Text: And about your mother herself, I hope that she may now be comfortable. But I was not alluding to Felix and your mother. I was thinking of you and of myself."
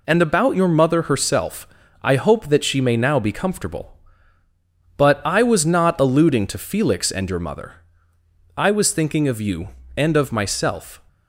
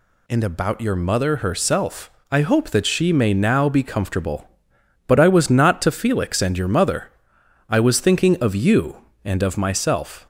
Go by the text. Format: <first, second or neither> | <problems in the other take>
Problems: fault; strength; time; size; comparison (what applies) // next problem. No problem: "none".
first | skips "alluding"; at 5.8 s